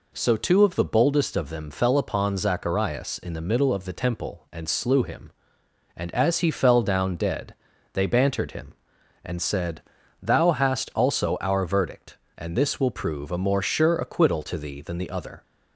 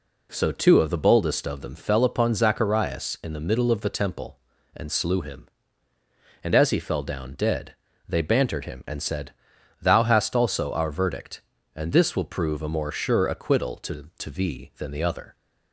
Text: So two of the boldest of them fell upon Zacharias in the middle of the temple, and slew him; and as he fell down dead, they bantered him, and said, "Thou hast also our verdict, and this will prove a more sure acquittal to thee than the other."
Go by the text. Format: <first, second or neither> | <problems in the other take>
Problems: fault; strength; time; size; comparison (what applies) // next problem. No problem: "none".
first | says "to" twice; at 14.1 s